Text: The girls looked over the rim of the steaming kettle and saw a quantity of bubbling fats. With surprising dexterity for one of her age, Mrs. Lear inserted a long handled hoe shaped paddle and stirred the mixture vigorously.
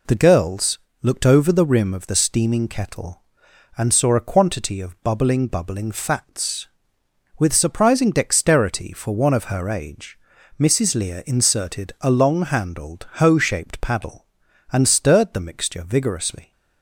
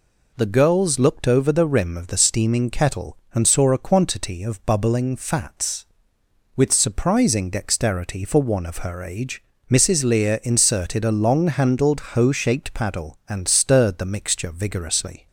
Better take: second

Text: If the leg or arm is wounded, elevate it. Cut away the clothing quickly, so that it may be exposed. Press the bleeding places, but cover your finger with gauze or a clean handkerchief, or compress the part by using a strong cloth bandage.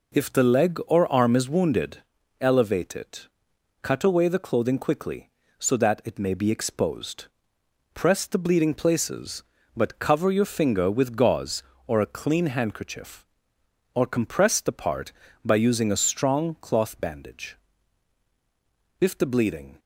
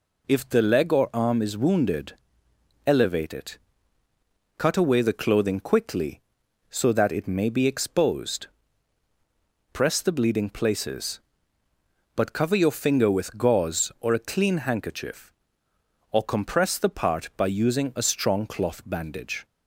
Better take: second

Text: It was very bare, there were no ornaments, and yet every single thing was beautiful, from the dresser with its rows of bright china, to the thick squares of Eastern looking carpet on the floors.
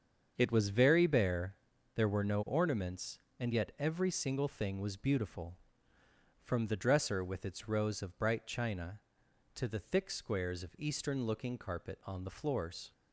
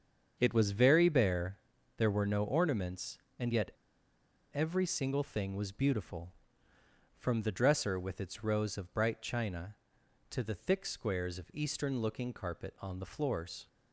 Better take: first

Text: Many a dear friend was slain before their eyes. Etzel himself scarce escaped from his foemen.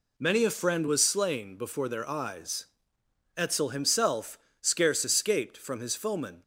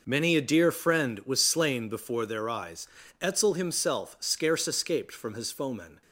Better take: second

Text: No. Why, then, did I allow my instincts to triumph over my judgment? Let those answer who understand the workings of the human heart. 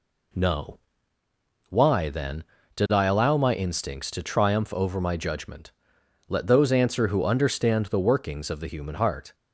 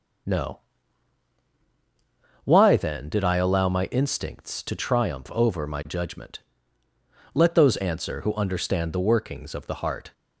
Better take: first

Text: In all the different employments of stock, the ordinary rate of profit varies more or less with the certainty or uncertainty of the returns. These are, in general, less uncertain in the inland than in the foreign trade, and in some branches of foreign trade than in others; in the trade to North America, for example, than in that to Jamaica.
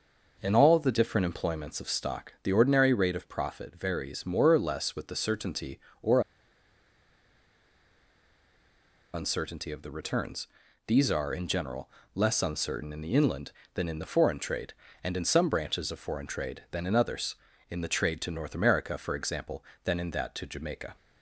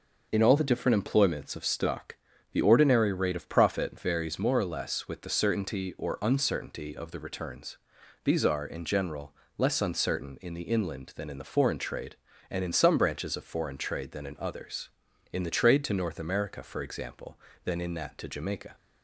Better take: second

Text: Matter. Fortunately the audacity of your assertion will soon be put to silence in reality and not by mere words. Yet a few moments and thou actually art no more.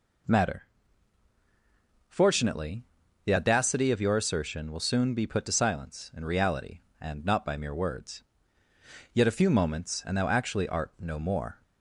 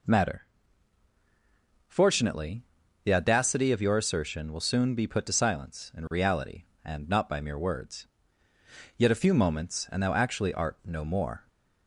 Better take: neither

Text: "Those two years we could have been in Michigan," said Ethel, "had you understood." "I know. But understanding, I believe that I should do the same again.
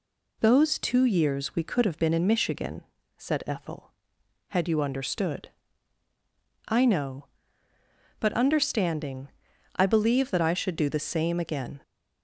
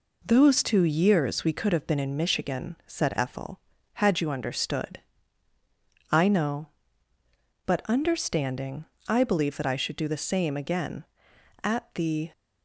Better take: first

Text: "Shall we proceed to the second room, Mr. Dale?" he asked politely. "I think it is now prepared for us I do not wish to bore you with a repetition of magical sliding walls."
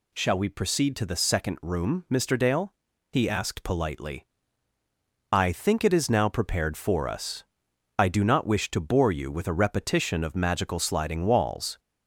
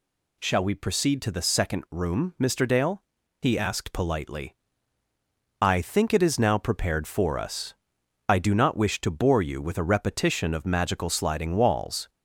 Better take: neither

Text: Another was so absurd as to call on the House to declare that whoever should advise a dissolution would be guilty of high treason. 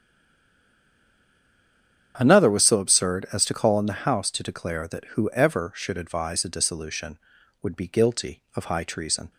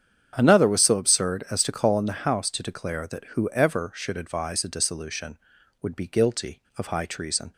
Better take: second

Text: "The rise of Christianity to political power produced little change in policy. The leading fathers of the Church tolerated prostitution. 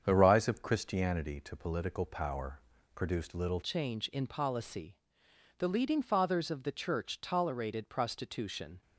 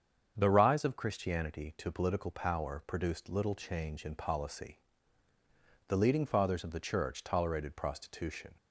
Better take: second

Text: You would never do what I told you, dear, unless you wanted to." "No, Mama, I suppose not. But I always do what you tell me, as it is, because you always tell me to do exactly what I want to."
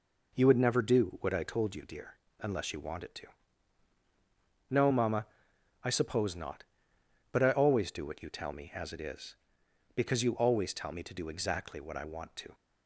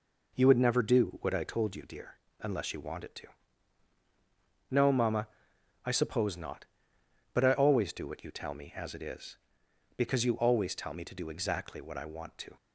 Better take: neither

